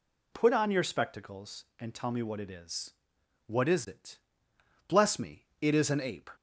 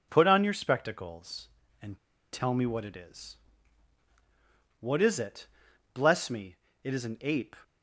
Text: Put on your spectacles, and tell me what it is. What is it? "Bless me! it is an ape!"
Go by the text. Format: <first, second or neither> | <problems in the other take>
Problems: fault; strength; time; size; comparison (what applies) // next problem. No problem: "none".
first | pauses between "and" and "tell"; slight; at 1.9 s; 0.34 s long